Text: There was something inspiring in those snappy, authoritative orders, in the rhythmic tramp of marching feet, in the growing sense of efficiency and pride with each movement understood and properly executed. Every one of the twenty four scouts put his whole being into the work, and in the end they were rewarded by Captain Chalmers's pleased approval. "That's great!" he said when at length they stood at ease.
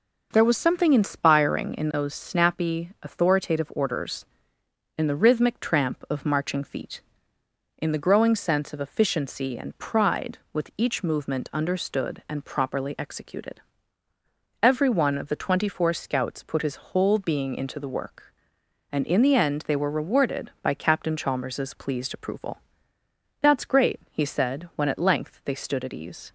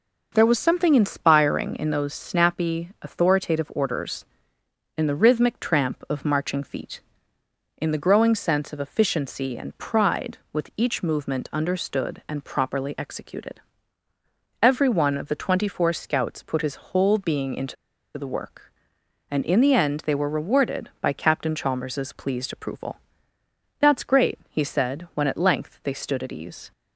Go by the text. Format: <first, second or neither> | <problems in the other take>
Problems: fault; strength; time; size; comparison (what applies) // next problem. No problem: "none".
first | pauses between "into" and "the"; at 17.7 s; 0.42 s long